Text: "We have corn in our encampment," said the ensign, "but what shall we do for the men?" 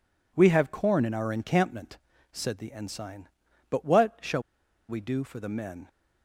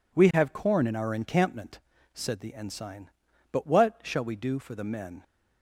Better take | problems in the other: second | pauses between "shall" and "we"; noticeable; at 4.4 s; 0.47 s long

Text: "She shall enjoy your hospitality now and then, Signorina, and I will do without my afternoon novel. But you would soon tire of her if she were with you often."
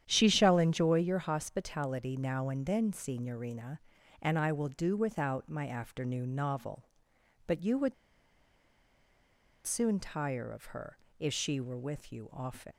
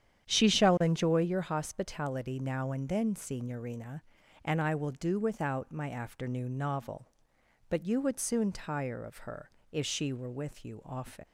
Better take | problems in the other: second | starts louder than the rest; strong; until 1.0 s; 9.5 dB; strong in the second // pauses between "would" and "soon"; strong; at 7.9 s; 1.7 s long // pauses between "her" and "if"; slight; at 10.9 s; 0.22 s long; slight in the second

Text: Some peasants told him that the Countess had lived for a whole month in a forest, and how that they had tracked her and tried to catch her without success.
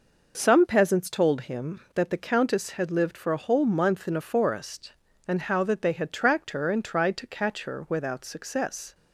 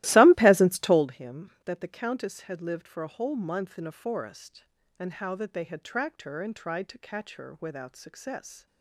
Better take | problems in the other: first | starts louder than the rest; strong; until 1.1 s; 16.5 dB

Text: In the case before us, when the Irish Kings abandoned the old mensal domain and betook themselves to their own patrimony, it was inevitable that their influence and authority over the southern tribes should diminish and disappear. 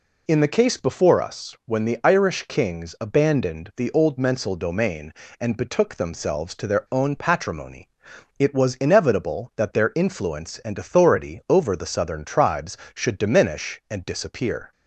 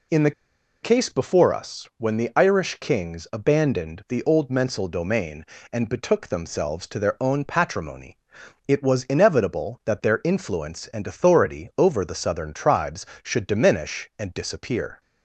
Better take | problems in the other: first | pauses between "the" and "case"; noticeable; at 0.3 s; 0.52 s long

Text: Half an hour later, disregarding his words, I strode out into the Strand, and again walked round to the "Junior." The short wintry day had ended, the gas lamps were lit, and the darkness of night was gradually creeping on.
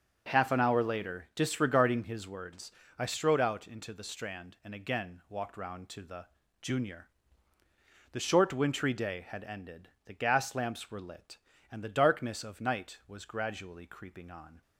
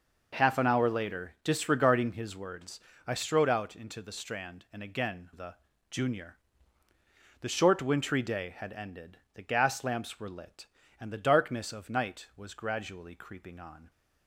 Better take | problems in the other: first | skips "walked round to"; at 5.3 s // pauses between "the" and "Junior"; at 5.5 s; 0.38 s long; also in the first

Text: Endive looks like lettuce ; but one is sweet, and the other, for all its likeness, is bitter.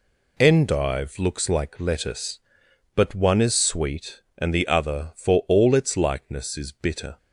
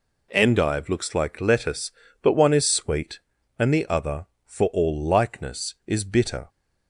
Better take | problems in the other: first | skips "its"; at 5.0 s

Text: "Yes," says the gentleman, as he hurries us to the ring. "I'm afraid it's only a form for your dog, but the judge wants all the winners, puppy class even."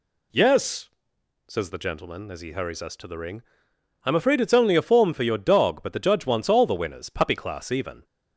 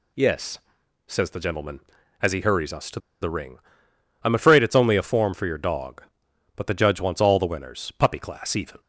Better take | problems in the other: first | pauses between "to" and "the"; slight; at 2.9 s; 0.22 s long

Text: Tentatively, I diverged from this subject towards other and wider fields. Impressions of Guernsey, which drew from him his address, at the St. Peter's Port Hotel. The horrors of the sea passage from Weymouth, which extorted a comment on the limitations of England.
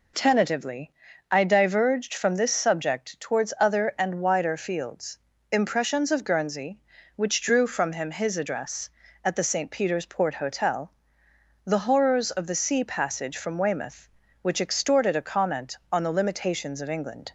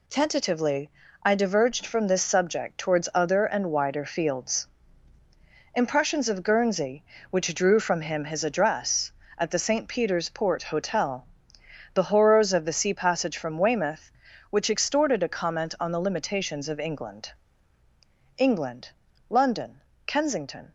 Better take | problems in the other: first | goes on to say "England London Kensington"; strong; from 18.3 s on; 2.3 s long

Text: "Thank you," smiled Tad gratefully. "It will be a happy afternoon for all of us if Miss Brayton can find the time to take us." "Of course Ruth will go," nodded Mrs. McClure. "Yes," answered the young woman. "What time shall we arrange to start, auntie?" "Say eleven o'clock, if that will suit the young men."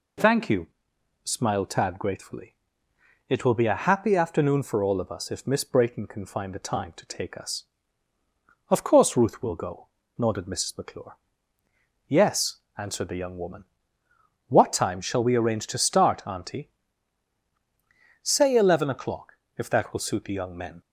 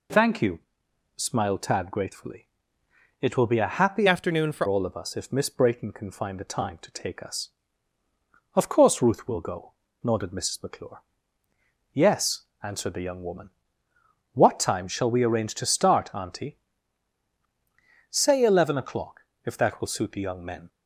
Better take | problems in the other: first | changes voice from "afternoon" to "for"; from 4.0 to 4.6 s; 0.6 s long

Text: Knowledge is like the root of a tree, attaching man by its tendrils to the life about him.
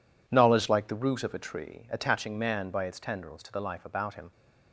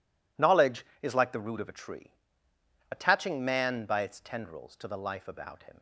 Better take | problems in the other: second | skips "is"; at 0.6 s

